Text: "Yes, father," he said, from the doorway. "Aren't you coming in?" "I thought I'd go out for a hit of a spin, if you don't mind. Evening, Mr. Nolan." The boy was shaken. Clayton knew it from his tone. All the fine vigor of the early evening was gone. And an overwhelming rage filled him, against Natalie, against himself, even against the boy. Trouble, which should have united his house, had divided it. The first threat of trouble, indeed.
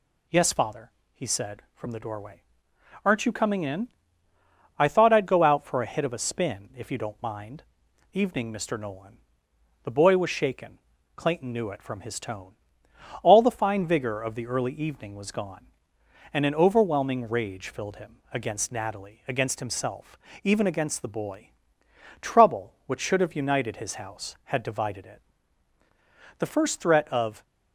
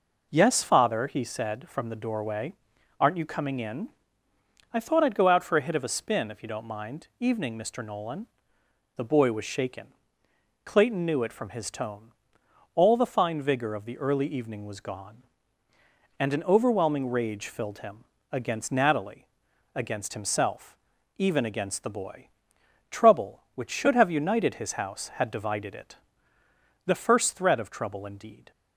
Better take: second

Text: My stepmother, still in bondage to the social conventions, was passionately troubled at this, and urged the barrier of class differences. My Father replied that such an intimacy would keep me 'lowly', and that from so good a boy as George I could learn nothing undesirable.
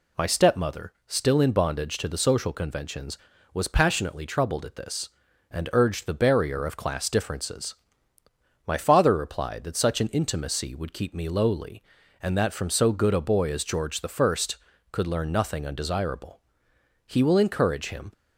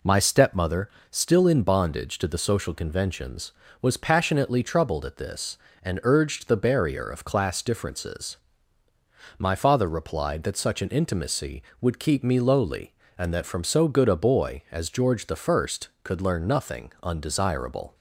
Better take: second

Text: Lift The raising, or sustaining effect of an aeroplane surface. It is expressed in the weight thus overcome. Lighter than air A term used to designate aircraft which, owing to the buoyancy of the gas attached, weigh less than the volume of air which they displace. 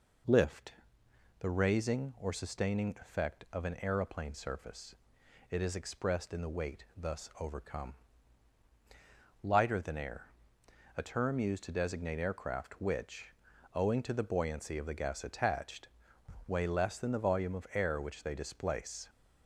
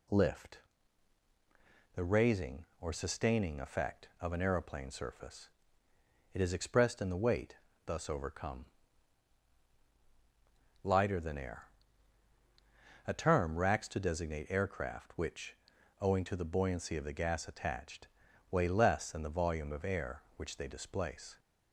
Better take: first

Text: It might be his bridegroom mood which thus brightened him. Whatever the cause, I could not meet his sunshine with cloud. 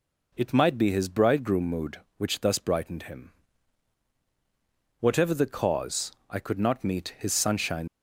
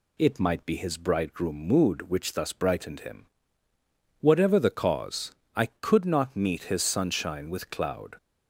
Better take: second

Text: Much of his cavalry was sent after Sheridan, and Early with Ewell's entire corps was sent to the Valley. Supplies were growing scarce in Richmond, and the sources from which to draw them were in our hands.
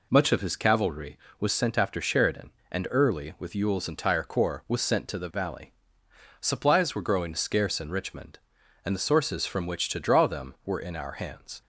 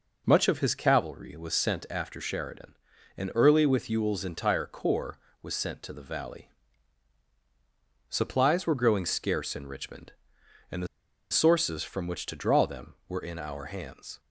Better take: first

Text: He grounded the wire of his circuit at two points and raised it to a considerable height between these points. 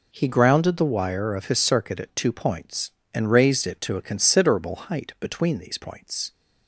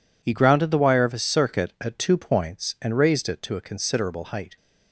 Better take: first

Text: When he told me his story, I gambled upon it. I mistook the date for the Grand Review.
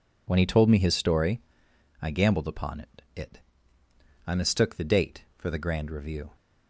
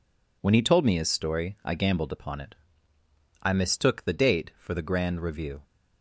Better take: second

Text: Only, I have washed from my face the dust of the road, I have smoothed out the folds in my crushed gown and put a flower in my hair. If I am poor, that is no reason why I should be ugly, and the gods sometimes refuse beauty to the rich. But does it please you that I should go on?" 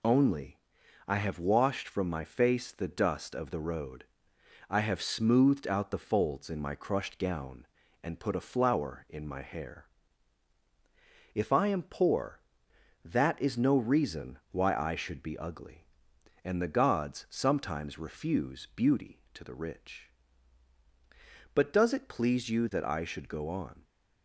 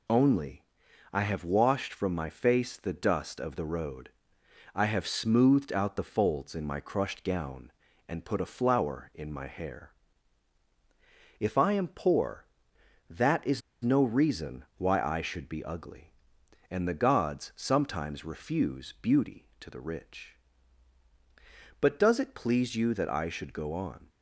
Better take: first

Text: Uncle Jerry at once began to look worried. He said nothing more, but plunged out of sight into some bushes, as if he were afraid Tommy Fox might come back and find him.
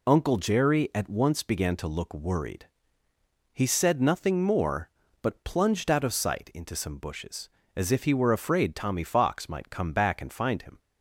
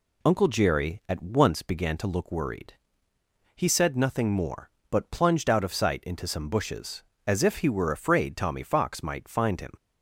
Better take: first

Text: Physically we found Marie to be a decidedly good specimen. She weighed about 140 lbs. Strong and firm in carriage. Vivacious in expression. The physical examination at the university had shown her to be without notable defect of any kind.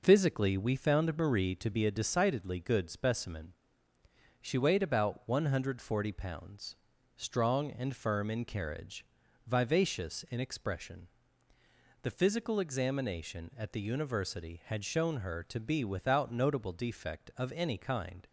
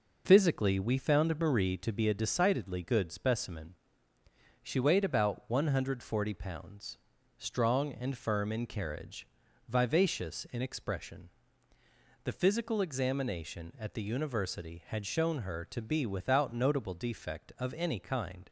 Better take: neither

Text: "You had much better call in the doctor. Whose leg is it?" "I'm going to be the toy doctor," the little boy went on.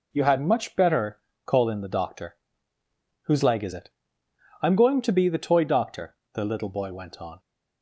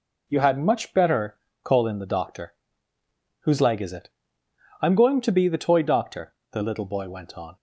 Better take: neither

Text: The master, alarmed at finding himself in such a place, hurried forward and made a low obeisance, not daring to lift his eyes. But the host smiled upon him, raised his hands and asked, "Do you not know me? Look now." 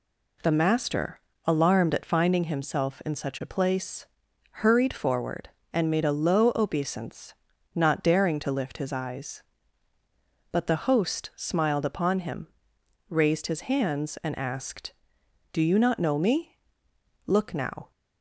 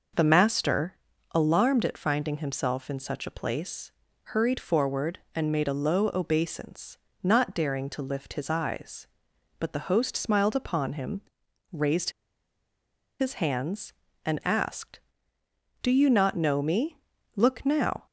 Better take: first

